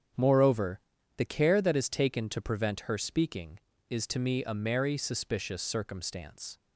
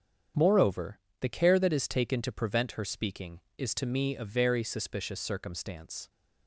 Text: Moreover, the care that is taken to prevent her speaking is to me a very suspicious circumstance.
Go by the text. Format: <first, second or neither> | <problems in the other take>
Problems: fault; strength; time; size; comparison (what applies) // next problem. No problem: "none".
second | starts louder than the rest; strong; until 1.5 s; 8 dB; strong in the second // says "merry" for "very"; at 4.5 s